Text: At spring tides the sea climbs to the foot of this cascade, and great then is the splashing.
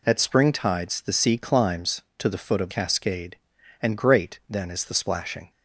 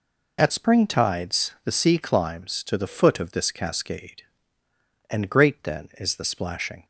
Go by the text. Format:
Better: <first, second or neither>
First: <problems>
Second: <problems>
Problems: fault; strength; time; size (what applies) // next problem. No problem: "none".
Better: second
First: skips "this"; at 2.7 s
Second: none